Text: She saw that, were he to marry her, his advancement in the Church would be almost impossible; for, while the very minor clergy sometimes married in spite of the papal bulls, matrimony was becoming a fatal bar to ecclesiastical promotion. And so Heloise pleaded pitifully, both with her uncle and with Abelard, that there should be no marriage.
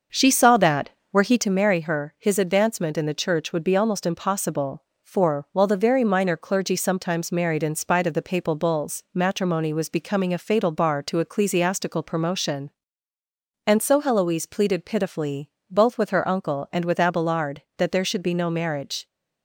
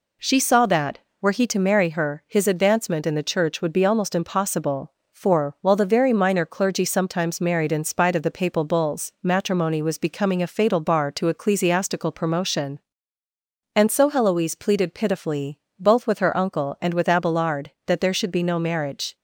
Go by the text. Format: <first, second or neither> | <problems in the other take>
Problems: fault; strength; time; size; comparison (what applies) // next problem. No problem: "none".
second | starts louder than the rest; until 1.5 s; 6.5 dB